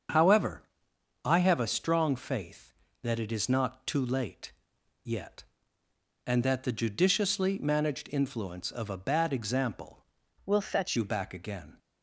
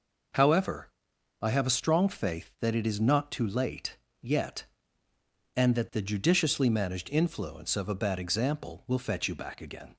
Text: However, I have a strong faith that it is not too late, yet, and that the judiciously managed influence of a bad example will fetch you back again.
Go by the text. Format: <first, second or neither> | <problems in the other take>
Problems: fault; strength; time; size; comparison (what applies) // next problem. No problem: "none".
second | starts louder than the rest; until 1.7 s; 7 dB // changes voice from "will" to "fetch"; from 10.4 to 10.9 s; 0.5 s long